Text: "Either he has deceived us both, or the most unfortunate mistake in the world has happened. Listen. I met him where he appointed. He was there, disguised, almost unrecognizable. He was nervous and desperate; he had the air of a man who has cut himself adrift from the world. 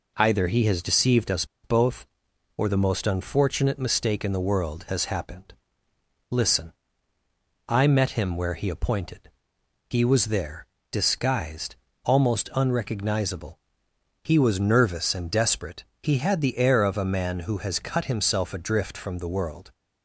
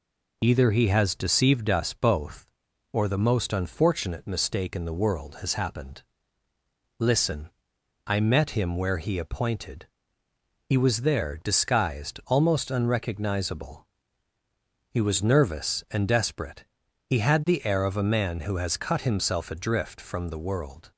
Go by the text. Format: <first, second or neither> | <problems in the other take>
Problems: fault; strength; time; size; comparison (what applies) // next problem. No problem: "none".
second | pauses between "us" and "both"; slight; at 1.4 s; 0.17 s long